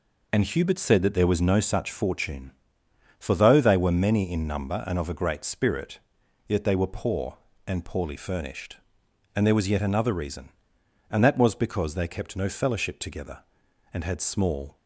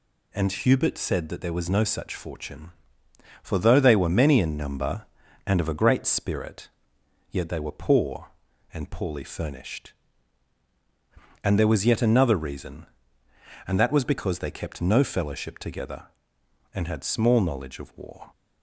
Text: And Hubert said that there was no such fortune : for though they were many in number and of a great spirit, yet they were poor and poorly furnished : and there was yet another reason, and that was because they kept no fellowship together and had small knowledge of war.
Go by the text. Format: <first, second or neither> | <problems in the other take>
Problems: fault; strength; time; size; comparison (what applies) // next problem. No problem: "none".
second | stops before "knowledge of war"; at 14.7 s